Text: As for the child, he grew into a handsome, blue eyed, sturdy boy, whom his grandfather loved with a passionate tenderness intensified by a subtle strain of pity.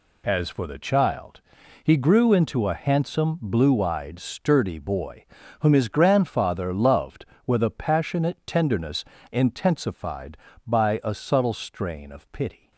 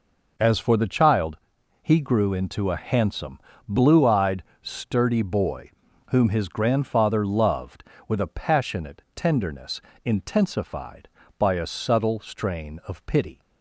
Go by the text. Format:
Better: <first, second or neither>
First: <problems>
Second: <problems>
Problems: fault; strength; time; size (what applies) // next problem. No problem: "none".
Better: neither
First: pauses between "tenderness" and "intensified"; slight; at 9.0 s; 0.26 s long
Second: pauses between "tenderness" and "intensified"; slight; at 9.8 s; 0.22 s long